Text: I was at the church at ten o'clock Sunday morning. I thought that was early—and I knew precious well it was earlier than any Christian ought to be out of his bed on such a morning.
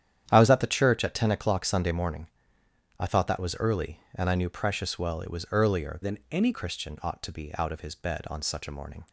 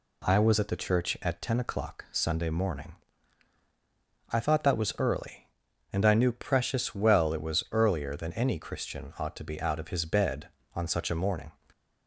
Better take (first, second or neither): second